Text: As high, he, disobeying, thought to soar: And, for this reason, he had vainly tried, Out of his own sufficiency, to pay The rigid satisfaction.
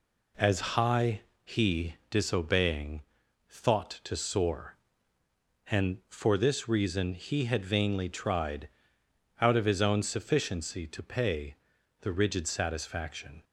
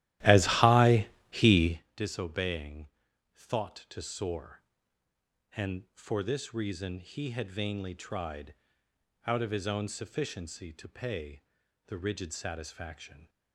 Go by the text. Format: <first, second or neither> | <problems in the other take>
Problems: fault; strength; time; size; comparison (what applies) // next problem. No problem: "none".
first | starts louder than the rest; strong; until 1.8 s; 14.5 dB // pauses between "pay" and "The"; noticeable; at 11.4 s; 0.46 s long; noticeable in the first